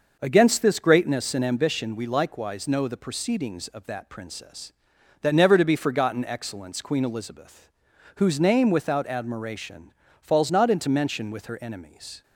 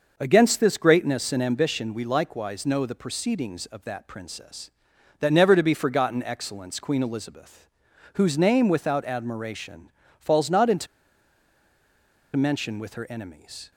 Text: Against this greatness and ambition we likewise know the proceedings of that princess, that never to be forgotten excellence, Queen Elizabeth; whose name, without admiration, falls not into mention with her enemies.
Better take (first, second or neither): first